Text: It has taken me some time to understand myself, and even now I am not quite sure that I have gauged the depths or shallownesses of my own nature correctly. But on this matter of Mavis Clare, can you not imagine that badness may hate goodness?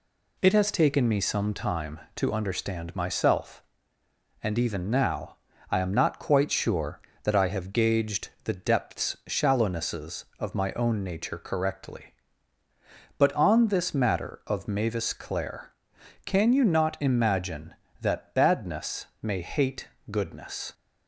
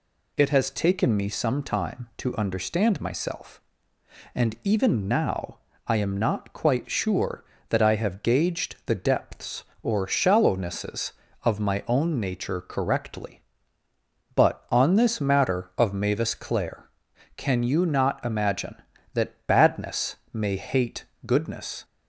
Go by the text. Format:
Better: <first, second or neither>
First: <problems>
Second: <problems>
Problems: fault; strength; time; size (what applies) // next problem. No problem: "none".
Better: second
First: pauses between "now" and "I"; slight; at 5.3 s; 0.34 s long // skips "or"; at 9.2 s // pauses between "badness" and "may"; slight; at 19.0 s; 0.16 s long // pauses between "hate" and "goodness"; slight; at 19.8 s; 0.24 s long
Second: pauses between "now" and "I"; slight; at 5.5 s; 0.28 s long // pauses between "badness" and "may"; slight; at 20.1 s; 0.16 s long // pauses between "hate" and "goodness"; slight; at 21.0 s; 0.22 s long